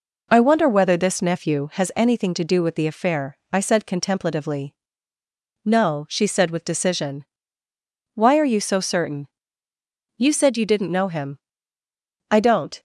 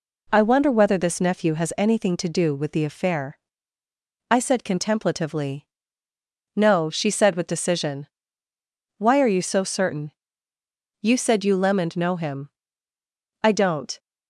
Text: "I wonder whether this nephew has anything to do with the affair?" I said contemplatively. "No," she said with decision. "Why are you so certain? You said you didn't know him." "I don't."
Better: first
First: none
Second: says "lemoned" for "didn't"; at 11.5 s

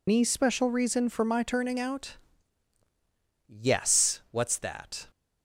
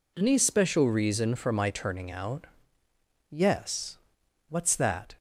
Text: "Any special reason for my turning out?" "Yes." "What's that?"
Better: second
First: loses the start of "Any"; at 0.0 s; 105 ms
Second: none

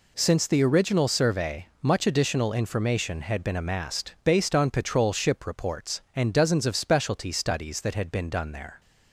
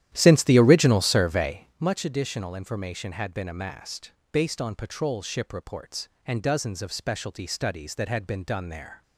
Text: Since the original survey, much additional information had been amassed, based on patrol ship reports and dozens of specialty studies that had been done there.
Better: first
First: none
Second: starts louder than the rest; strong; until 1.9 s; 12 dB

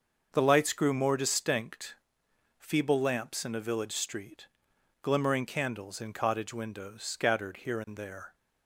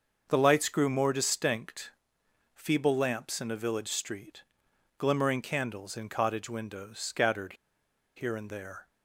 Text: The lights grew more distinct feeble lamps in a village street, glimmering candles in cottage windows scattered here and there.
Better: first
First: starts louder than the rest; until 1.3 s; 6 dB // pauses between "distinct" and "feeble"; noticeable; at 1.9 s; 0.62 s long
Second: starts louder than the rest; until 1.3 s; 6 dB // pauses between "distinct" and "feeble"; noticeable; at 1.9 s; 0.62 s long // pauses between "scattered" and "here"; noticeable; at 7.5 s; 0.62 s long

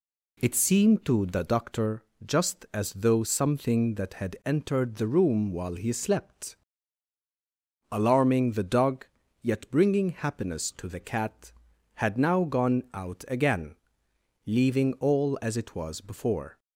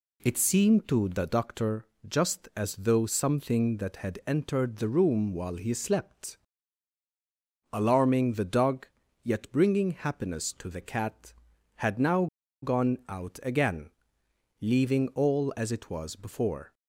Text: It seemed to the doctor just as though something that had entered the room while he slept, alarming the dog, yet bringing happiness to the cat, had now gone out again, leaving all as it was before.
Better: first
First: pauses between "doctor" and "just"; slight; at 2.0 s; 0.20 s long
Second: pauses between "doctor" and "just"; slight; at 1.8 s; 0.20 s long // pauses between "now" and "gone"; at 12.2 s; 0.36 s long

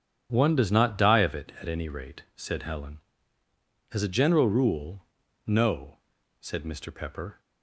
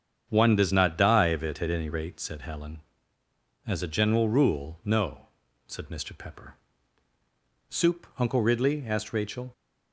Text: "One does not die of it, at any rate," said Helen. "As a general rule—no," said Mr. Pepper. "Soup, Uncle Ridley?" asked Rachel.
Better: second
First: starts louder than the rest; strong; until 1.3 s; 9 dB // stops before "Soup Uncle Ridley asked Rachel"; at 7.4 s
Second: starts louder than the rest; strong; until 1.3 s; 8 dB

